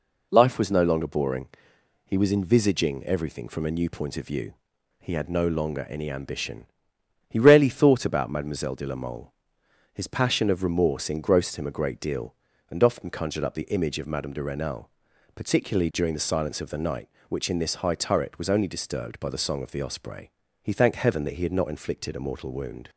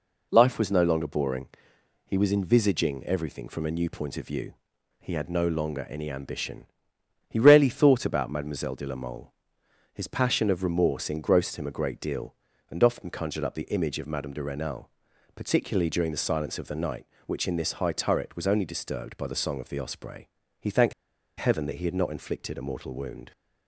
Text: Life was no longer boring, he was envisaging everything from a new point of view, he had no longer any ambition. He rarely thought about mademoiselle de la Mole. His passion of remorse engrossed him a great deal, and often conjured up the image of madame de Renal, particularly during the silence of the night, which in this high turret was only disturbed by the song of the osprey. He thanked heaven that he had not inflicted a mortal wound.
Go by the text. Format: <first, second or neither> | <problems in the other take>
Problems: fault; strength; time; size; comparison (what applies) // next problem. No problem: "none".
first | pauses between "thanked" and "heaven"; noticeable; at 20.9 s; 0.46 s long